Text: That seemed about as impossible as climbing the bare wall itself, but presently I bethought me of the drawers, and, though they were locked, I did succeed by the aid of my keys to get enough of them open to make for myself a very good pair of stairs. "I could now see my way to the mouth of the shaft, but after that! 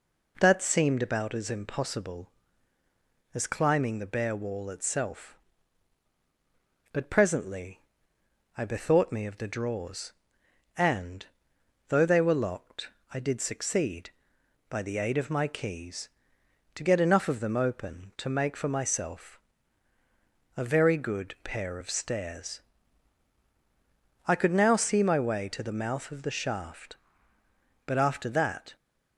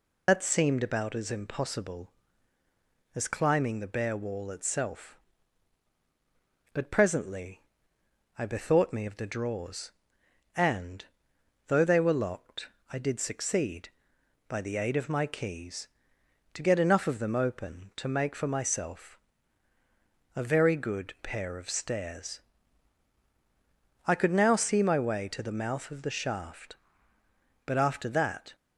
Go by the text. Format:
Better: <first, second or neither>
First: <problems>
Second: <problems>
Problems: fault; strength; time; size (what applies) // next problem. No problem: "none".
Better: first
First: pauses between "presently" and "I"; noticeable; at 7.7 s; 0.76 s long // pauses between "myself" and "a"; at 19.3 s; 1.1 s long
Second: loses the start of "That"; at 0.2 s; 115 ms // pauses between "presently" and "I"; noticeable; at 7.6 s; 0.76 s long // pauses between "myself" and "a"; at 19.1 s; 1.1 s long